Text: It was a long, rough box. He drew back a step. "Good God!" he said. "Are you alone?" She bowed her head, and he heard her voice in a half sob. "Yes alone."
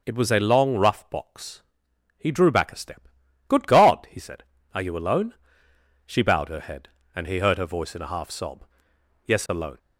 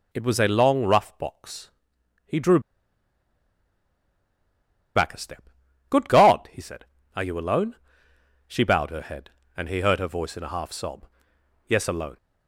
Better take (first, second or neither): first